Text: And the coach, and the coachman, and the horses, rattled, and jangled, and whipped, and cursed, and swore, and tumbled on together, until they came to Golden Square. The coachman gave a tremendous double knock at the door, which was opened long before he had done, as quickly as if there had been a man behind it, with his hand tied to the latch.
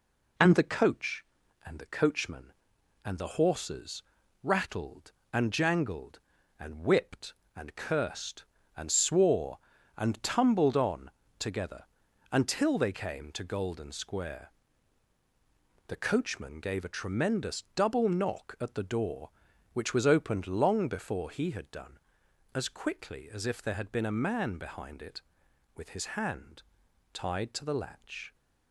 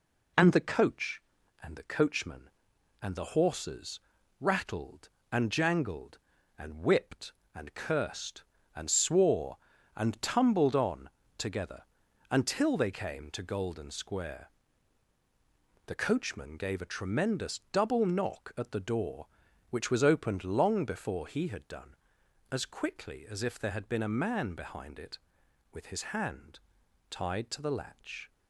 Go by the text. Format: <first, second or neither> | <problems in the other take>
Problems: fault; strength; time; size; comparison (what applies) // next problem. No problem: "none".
neither | pauses between "on" and "together"; slight; the same in both // pauses between "hand" and "tied"; noticeable; the same in both